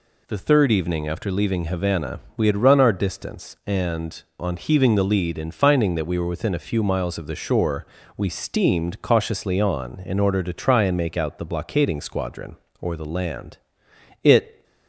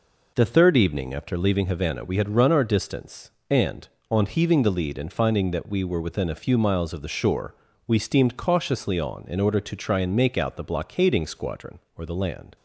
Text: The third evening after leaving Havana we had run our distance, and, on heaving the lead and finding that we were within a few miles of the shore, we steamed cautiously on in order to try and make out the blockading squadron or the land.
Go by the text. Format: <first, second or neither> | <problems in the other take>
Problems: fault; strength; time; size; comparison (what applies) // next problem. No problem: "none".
second | pauses between "Havana" and "we"; slight; at 2.1 s; 0.16 s long // goes on to say "It"; slight; from 14.2 s on; 0.40 s long